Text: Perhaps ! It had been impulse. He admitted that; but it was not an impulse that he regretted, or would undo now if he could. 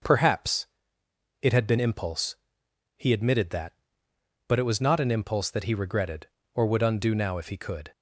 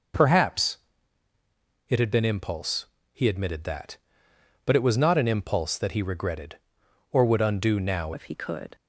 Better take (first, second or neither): first